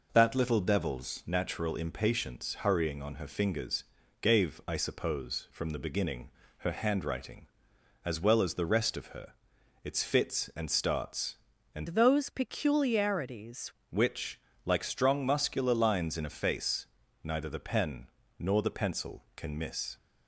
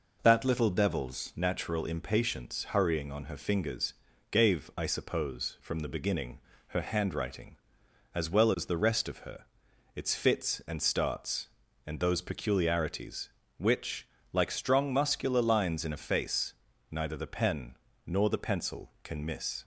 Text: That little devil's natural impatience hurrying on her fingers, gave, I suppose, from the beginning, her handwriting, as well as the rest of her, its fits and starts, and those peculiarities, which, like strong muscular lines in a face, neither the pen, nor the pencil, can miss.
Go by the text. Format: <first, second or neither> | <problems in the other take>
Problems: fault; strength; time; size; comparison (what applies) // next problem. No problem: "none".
second | changes voice from "those" to "peculiarities"; from 11.8 to 13.7 s; 1.9 s long